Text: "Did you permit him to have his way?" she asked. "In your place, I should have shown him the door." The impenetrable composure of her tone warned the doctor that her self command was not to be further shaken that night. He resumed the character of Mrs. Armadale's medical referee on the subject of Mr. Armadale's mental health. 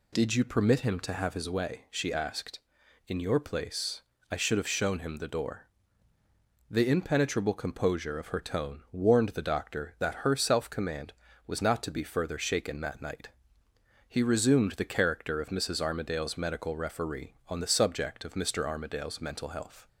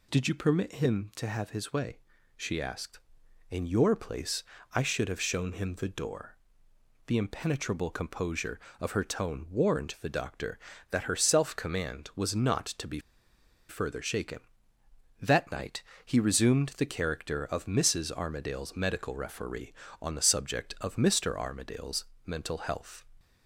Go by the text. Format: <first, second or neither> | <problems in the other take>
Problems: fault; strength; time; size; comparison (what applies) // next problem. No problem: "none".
first | pauses between "be" and "further"; noticeable; at 12.9 s; 0.69 s long // pauses between "Armadale's" and "mental"; slight; at 22.0 s; 0.22 s long